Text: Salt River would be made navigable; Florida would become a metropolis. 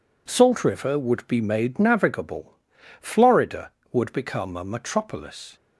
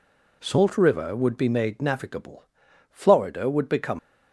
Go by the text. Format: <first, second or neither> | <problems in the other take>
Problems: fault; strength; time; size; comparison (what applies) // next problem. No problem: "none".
first | stops before "a metropolis"; at 3.9 s